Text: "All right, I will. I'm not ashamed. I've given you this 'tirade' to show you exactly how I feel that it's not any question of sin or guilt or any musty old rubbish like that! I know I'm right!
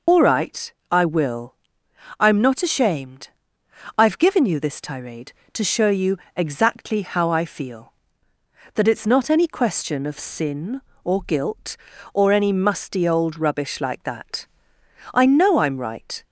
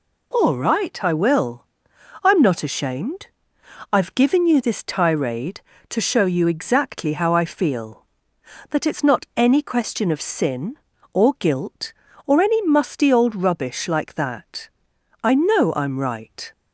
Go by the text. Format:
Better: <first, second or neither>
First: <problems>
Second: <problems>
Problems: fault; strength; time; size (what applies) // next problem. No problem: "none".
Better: second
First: loses the start of "All"; at 0.0 s; 85 ms // pauses between "you" and "exactly"; slight; at 6.1 s; 0.18 s long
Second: none